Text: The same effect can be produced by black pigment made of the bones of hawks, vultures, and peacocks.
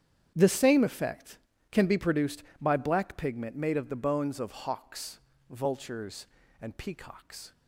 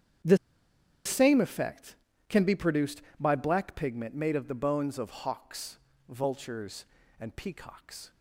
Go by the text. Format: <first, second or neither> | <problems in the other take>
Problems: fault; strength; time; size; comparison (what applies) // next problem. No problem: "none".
first | starts louder than the rest; strong; until 1.9 s; 9 dB; strong in the first // pauses between "The" and "same"; noticeable; at 0.3 s; 0.69 s long